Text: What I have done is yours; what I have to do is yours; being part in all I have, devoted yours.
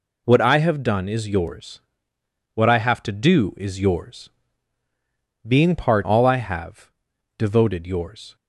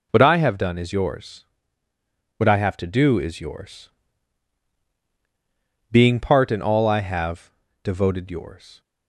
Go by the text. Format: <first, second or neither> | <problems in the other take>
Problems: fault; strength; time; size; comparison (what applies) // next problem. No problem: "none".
second | skips "in"; at 6.0 s